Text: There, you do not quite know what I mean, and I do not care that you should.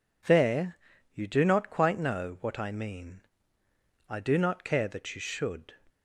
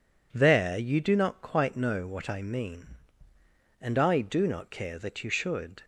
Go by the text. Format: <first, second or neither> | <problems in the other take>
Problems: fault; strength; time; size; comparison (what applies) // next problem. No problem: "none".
second | skips "and"; at 3.6 s